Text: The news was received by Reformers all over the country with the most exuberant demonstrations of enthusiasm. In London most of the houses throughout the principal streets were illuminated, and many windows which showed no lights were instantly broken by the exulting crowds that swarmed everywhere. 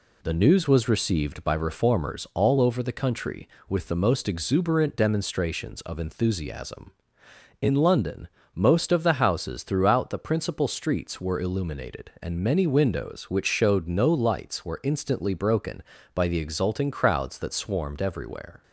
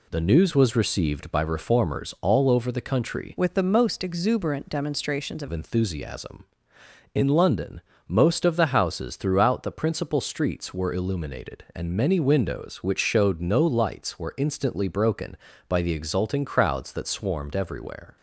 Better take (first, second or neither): first